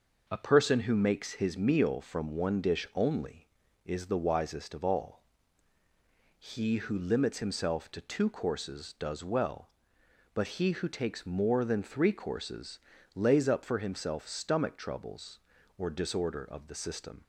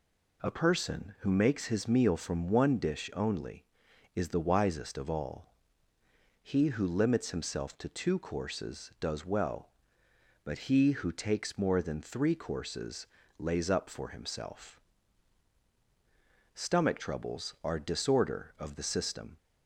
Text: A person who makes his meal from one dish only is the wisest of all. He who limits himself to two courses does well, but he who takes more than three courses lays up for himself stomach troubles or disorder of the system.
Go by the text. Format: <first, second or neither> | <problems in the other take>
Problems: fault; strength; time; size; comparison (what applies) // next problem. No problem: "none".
first | pauses between "courses" and "lays"; slight; at 13.0 s; 0.34 s long; slight in the first // pauses between "himself" and "stomach"; strong; at 14.7 s; 1.7 s long // says "are" for "or"; at 17.6 s